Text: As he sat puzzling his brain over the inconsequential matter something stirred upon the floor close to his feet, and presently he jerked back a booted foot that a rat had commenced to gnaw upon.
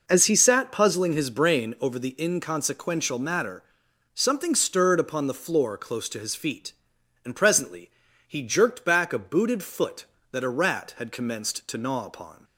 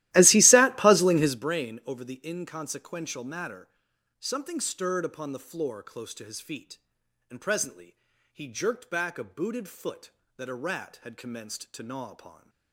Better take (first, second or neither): first